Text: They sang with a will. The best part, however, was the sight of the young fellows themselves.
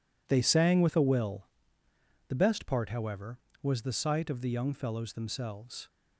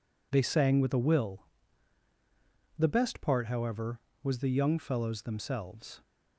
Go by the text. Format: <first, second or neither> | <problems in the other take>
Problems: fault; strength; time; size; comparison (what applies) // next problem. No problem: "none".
first | skips "sight of the"; at 4.4 s